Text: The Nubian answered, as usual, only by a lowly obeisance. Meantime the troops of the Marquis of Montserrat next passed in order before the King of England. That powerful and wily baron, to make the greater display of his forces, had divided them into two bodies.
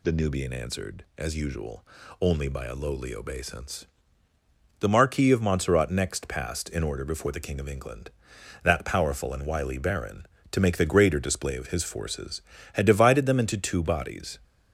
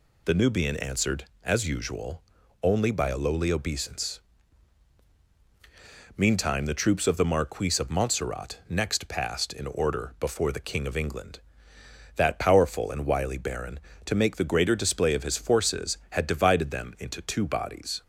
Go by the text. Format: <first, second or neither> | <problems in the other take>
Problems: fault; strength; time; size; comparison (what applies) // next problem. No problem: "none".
second | skips "Meantime the troops of"; at 4.3 s